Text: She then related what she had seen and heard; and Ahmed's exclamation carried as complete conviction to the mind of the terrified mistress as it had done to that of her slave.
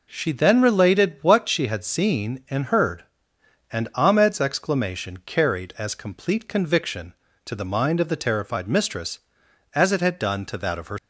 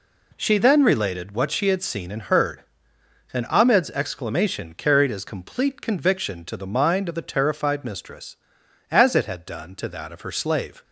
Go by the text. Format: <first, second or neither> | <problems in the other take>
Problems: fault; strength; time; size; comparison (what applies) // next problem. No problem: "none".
second | stops before "slave"; at 10.9 s